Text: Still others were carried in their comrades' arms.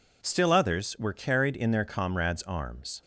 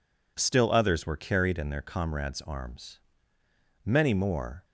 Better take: first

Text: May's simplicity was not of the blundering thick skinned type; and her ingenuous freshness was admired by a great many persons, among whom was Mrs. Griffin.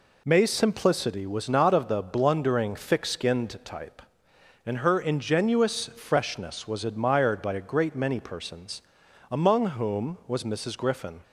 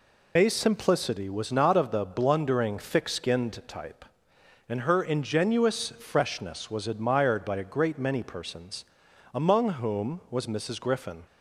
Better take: first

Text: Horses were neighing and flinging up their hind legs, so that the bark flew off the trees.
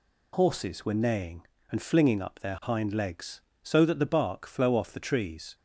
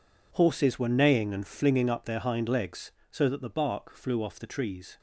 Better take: second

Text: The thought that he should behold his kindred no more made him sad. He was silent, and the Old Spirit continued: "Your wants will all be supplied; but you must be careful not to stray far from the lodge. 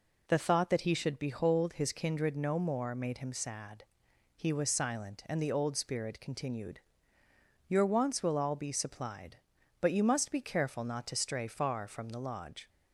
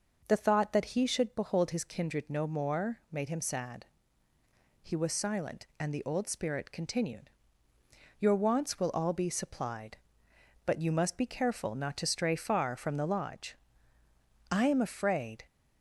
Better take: first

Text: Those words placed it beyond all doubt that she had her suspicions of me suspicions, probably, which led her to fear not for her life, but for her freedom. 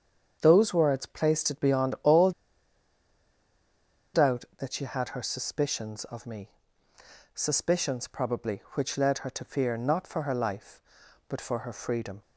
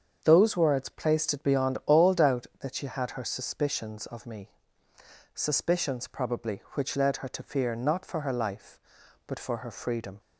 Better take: second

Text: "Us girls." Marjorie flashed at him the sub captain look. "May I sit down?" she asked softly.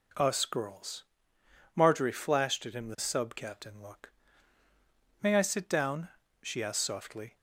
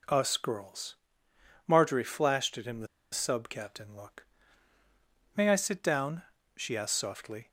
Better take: first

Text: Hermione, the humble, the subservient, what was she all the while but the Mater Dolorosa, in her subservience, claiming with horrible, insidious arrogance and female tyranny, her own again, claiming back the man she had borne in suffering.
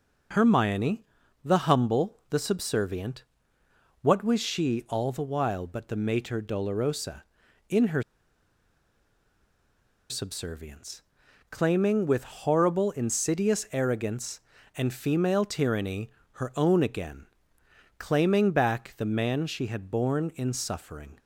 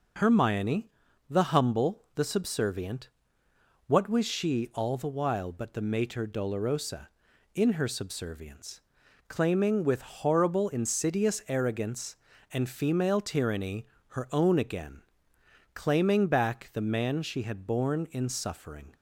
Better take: second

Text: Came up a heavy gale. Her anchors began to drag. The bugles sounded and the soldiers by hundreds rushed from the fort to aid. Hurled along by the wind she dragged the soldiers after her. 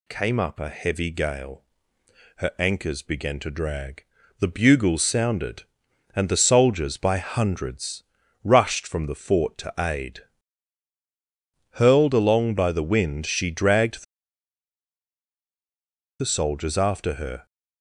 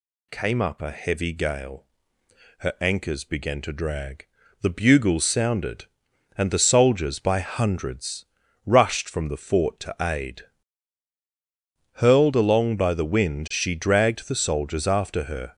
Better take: second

